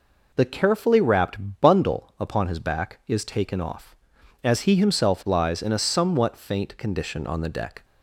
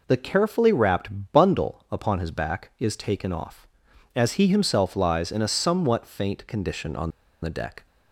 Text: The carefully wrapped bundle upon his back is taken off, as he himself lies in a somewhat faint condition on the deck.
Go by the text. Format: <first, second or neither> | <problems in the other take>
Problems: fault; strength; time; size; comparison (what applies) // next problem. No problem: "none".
first | pauses between "on" and "the"; slight; at 7.1 s; 0.32 s long